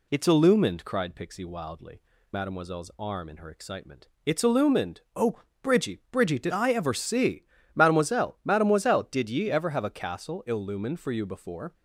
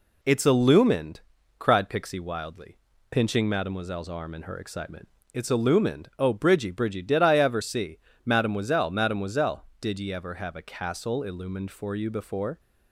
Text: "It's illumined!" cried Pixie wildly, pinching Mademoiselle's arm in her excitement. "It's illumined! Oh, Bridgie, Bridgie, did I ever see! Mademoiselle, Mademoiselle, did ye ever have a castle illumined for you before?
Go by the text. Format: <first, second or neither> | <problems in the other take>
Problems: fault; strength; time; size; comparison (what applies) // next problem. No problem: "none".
second | skips "pinching"; at 2.1 s